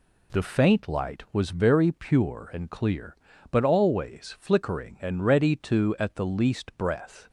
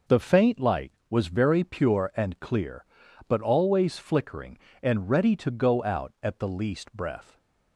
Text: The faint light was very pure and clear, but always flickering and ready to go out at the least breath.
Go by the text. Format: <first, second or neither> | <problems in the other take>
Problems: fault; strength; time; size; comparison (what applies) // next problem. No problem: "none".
second | skips "go out"; at 5.9 s